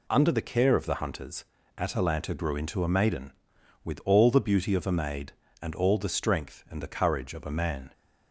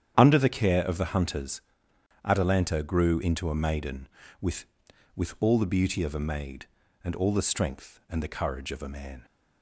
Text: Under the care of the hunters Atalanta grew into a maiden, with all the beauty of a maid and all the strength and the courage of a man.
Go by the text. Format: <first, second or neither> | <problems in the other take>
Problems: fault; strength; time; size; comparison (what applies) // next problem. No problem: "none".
first | starts louder than the rest; strong; until 1.1 s; 9.5 dB // pauses between "hunters" and "Atalanta"; noticeable; at 1.6 s; 0.62 s long; slight in the first // says "with" twice; at 5.1 s